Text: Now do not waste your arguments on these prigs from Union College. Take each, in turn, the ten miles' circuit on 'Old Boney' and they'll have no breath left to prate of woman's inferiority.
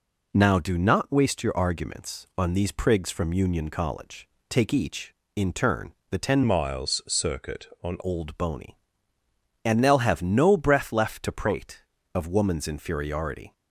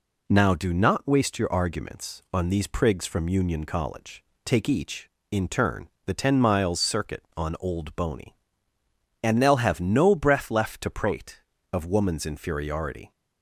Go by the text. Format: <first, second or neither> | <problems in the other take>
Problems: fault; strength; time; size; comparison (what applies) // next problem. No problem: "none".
second | changes voice from "miles" to "on"; from 6.4 to 7.9 s; 1.5 s long